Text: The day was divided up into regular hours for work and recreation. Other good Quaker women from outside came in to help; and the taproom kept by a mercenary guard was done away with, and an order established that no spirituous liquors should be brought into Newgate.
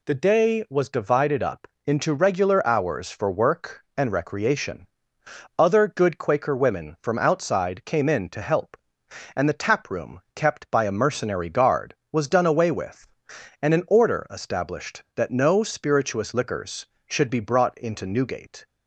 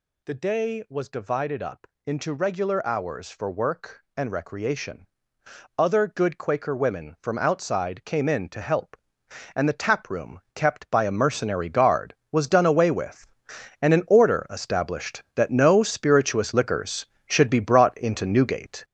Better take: first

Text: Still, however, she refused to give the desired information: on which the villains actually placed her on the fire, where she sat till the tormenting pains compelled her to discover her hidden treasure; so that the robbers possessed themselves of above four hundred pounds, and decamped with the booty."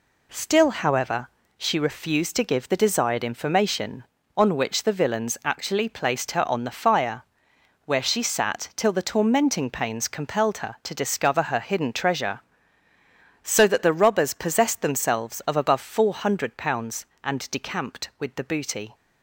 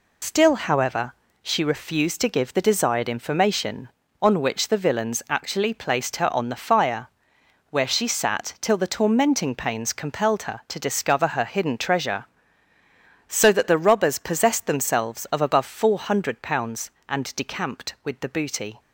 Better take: first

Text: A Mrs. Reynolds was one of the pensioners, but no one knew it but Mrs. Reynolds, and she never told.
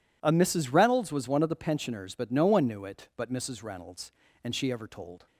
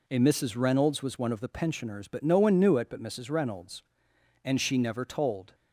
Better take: second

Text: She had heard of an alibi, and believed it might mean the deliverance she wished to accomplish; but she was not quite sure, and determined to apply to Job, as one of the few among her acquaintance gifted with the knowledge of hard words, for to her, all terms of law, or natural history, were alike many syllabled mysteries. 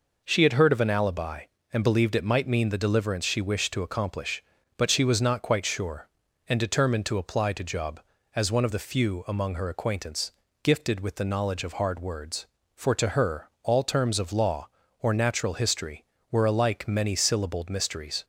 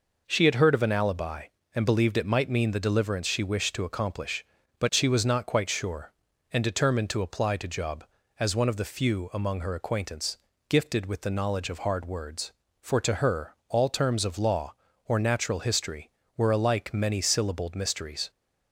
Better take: neither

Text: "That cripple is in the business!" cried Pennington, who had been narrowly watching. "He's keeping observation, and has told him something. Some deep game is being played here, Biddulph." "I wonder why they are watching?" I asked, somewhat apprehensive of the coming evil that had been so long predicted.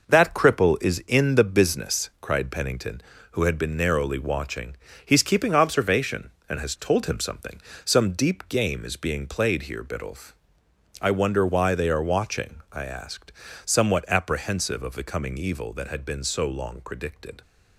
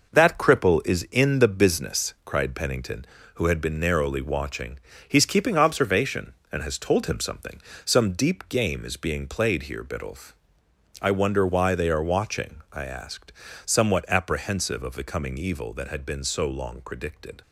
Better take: neither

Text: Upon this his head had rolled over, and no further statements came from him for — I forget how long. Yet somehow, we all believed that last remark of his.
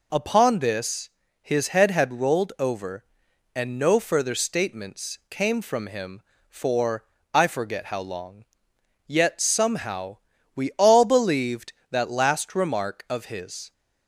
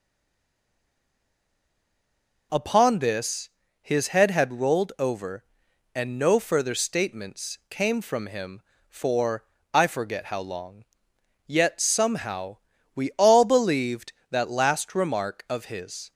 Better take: first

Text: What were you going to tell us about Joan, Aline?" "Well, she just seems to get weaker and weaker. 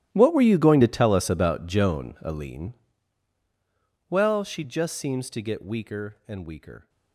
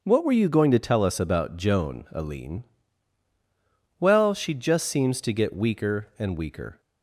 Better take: second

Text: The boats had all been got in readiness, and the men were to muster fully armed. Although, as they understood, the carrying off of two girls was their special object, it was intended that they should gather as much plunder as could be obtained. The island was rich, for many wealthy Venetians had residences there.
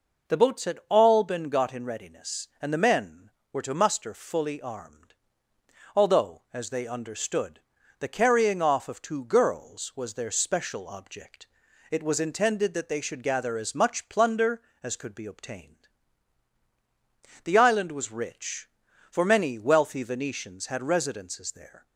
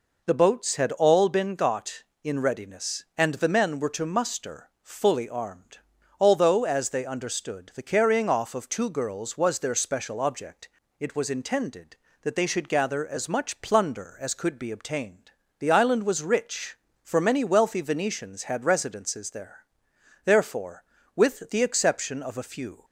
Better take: first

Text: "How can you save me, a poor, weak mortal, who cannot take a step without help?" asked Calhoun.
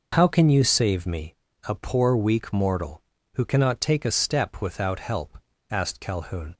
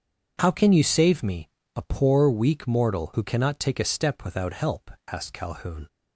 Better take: neither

